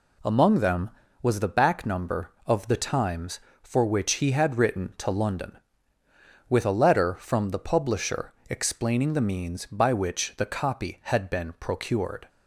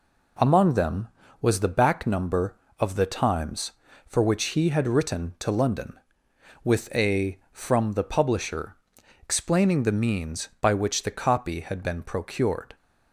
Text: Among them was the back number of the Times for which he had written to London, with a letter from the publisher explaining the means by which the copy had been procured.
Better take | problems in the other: first | skips "letter"; at 7.4 s // pauses between "publisher" and "explaining"; noticeable; at 8.7 s; 0.46 s long; slight in the first

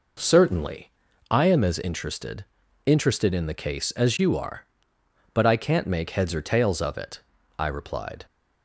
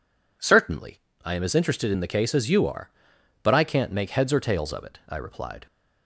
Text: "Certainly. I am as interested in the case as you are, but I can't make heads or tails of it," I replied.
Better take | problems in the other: second | says "interested" twice; at 2.8 s

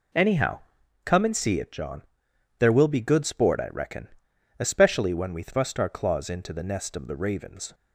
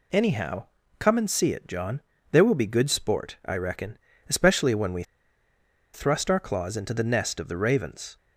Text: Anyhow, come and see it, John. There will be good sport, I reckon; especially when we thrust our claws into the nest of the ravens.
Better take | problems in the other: first | pauses between "we" and "thrust"; noticeable; at 5.0 s; 0.91 s long

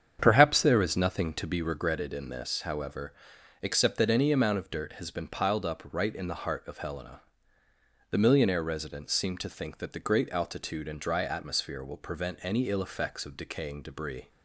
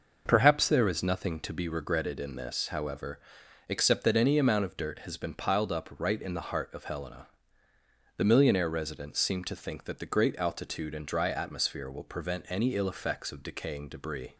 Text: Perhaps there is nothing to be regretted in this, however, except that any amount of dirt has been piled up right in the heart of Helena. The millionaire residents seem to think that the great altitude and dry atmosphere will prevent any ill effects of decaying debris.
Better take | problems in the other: second | starts louder than the rest; strong; until 1.9 s; 8 dB

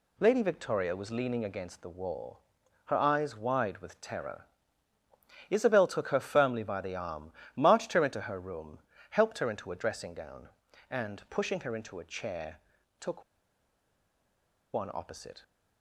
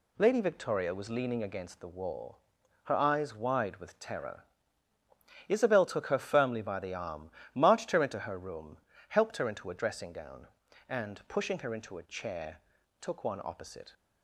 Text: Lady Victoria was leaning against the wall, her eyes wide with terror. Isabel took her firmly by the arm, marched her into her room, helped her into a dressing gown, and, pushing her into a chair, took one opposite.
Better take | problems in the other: second | pauses between "took" and "one"; strong; at 13.2 s; 1.5 s long

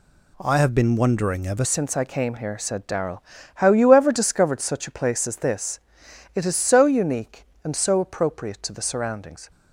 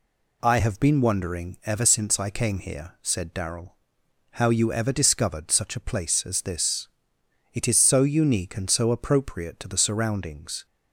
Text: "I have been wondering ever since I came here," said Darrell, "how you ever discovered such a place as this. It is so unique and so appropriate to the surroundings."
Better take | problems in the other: second | changes voice at "since"; from 1.6 s on; 7.9 s long

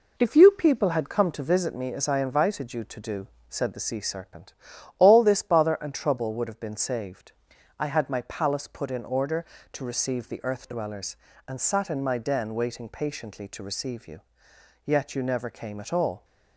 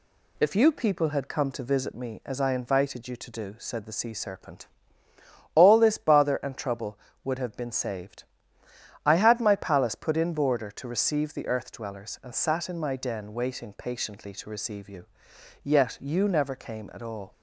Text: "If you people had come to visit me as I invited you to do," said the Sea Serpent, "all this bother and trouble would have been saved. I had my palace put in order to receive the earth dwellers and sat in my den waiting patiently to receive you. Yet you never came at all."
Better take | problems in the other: first | says "border" for "order"; at 10.3 s

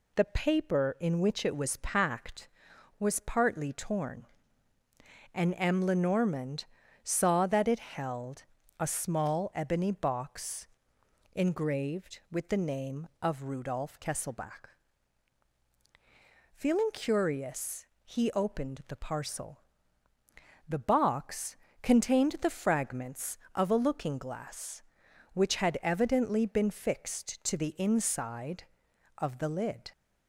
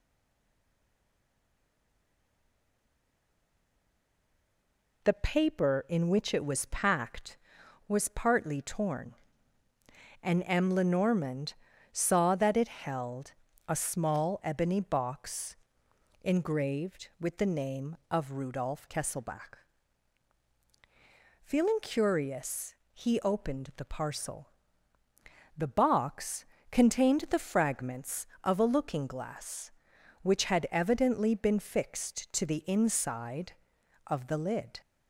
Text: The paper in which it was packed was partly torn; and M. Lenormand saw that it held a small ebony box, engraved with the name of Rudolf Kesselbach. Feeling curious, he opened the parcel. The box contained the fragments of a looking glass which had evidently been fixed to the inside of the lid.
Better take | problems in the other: first | stays silent before the first word; strong; until 5.0 s; 5.0 s long // pauses between "Lenormand" and "saw"; at 11.5 s; 0.38 s long; also in the first // pauses between "held" and "a"; slight; at 13.3 s; 0.34 s long; slight in the first // pauses between "box" and "contained"; slight; at 26.4 s; 0.26 s long; slight in the first

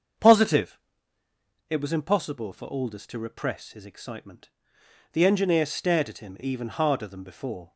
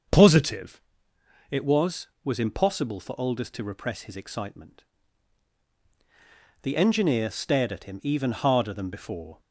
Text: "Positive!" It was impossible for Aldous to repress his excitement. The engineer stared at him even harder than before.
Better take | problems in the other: first | starts louder than the rest; until 1.8 s; 6.5 dB; also in the first // says "was" twice; at 2.2 s

